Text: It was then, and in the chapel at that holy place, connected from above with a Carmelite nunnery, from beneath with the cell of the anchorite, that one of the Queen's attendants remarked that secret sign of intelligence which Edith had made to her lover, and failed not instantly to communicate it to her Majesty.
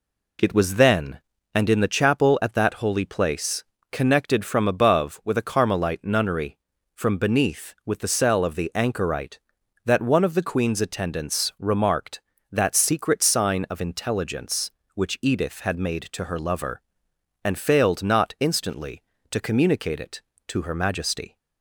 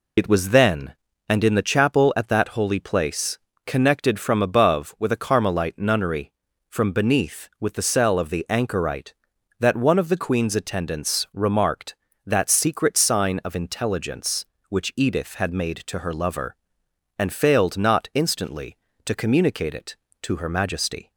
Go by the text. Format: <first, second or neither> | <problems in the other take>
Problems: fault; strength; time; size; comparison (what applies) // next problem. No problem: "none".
first | loses the start of "It"; at 0.1 s; 40 ms